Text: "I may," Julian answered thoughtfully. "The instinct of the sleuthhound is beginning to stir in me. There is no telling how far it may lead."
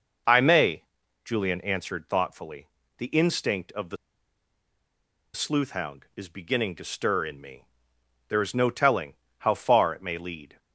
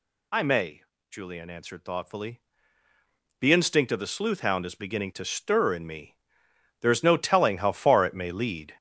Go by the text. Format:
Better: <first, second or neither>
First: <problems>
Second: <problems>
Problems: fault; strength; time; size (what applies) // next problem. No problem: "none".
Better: second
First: pauses between "the" and "sleuthhound"; strong; at 3.9 s; 1.3 s long // pauses between "telling" and "how"; slight; at 9.1 s; 0.22 s long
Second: none